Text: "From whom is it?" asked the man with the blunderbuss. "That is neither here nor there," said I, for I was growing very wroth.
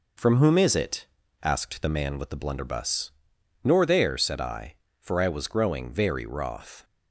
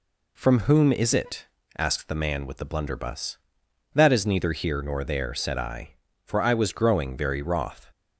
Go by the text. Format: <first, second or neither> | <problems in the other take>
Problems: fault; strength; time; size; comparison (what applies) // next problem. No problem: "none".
second | skips "That is neither here"; at 3.3 s